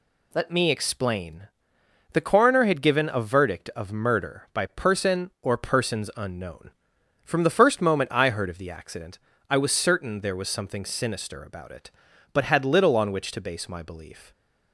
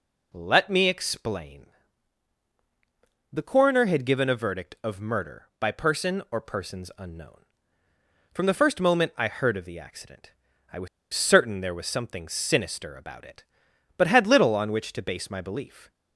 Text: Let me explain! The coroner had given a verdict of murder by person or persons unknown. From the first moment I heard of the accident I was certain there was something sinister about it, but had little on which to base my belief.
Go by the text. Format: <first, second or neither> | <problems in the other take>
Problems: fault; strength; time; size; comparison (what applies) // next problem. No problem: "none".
first | pauses between "accident" and "I"; at 10.3 s; 0.40 s long; slight in the first // pauses between "was" and "certain"; slight; at 10.8 s; 0.26 s long